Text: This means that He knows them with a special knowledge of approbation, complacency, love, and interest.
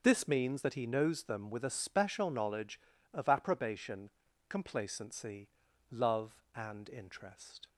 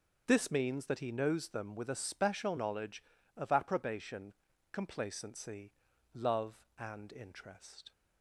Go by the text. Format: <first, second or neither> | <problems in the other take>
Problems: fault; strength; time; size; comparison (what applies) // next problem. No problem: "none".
neither | none